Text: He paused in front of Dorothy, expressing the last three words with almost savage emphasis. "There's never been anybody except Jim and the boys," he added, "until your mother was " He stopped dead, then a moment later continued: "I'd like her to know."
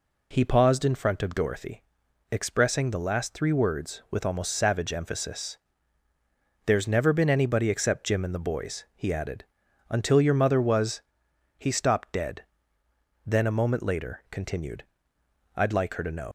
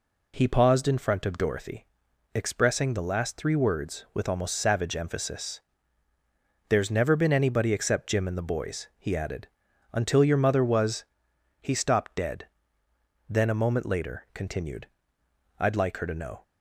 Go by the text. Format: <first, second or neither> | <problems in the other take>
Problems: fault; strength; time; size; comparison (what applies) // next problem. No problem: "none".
second | leaves "know" unfinished; at 16.2 s; 80 ms